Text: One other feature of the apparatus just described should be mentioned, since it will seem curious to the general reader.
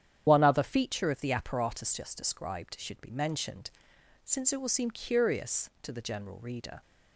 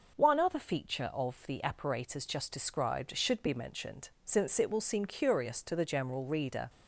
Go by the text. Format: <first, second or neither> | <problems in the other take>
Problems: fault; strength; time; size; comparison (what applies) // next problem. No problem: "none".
second | loses the start of "One"; at 0.2 s; 80 ms // starts louder than the rest; strong; until 1.2 s; 9.5 dB